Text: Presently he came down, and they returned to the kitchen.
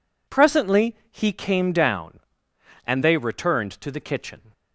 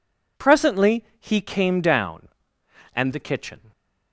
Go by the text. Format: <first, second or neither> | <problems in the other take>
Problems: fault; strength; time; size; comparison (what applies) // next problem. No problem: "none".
first | skips "they returned to"; at 3.1 s